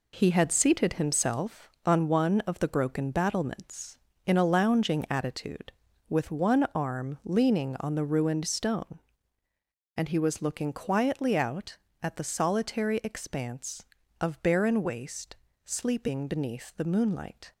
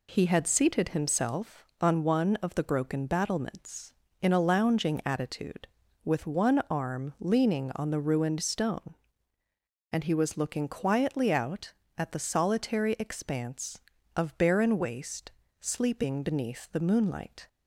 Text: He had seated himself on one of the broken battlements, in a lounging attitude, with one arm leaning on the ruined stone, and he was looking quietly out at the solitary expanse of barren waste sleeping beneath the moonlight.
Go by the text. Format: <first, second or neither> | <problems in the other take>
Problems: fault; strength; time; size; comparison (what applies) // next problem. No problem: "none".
second | gets quieter; throughout; 7 dB // pauses between "waste" and "sleeping"; slight; at 15.3 s; 0.30 s long; slight in the second